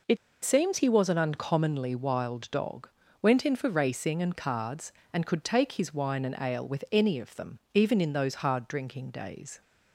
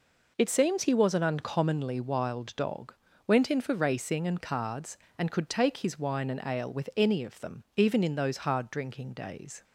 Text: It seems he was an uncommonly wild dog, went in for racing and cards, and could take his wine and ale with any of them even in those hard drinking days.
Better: second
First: pauses between "It" and "seems"; slight; at 0.1 s; 0.27 s long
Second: none

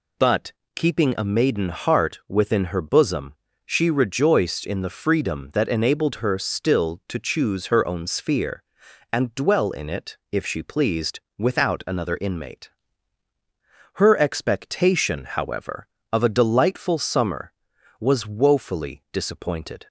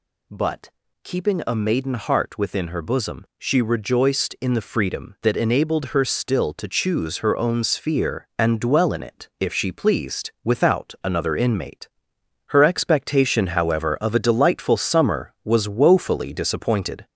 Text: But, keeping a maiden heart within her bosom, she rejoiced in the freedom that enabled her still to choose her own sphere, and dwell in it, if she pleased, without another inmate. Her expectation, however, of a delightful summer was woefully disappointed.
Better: first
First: none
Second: gets louder; slight; throughout; 3 dB

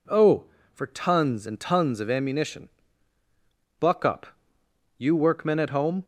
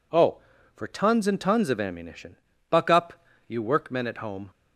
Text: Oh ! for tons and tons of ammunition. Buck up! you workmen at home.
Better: neither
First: none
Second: none

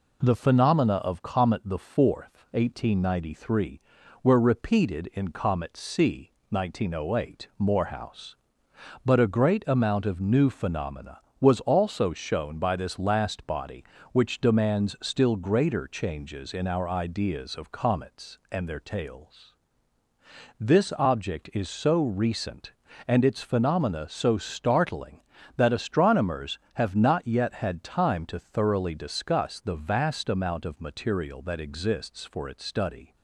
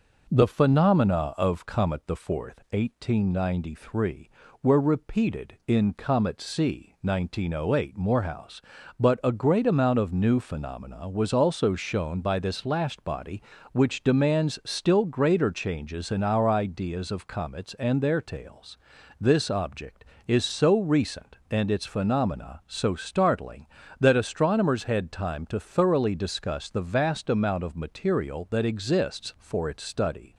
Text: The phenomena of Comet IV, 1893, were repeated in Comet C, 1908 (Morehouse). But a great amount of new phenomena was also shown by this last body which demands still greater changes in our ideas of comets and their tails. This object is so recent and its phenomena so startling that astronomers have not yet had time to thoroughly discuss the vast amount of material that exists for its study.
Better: first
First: none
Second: skips "have not yet"; at 24.8 s

